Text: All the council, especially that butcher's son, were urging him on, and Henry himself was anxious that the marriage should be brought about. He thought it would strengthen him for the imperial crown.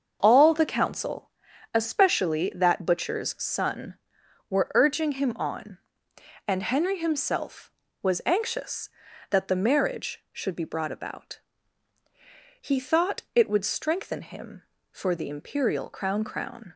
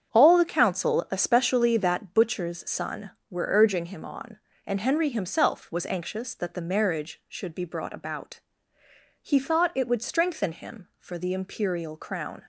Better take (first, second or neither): second